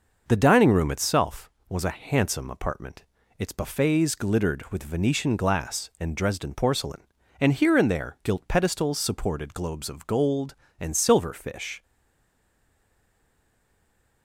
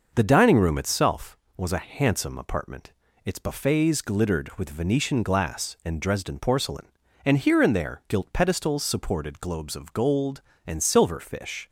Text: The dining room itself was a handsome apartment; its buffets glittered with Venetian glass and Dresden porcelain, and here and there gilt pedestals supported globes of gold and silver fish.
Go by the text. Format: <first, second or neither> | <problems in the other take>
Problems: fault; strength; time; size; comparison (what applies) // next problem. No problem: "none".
second | stays silent after the last word; from 11.8 s on; 2.4 s long